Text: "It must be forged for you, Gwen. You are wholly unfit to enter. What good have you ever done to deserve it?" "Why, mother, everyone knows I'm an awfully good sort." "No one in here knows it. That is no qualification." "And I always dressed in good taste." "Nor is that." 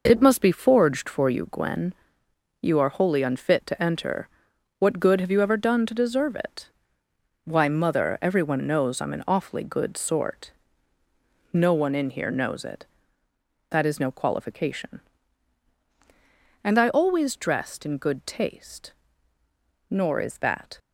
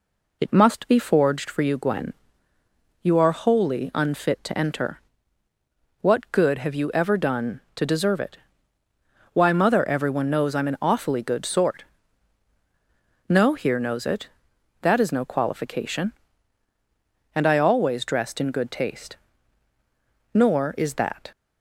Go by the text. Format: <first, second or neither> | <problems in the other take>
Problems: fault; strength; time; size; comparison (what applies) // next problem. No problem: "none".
first | skips "one in"; at 13.5 s